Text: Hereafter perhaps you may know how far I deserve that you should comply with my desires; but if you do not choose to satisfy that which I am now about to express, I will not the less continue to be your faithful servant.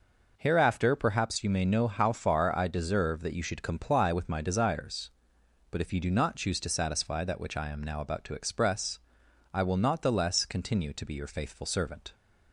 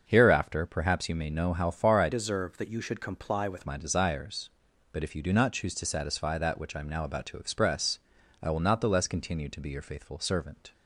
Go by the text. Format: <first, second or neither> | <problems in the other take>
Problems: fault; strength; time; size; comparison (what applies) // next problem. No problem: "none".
first | starts louder than the rest; until 1.0 s; 6.5 dB // changes voice from "deserve" to "with"; from 2.1 to 3.6 s; 1.5 s long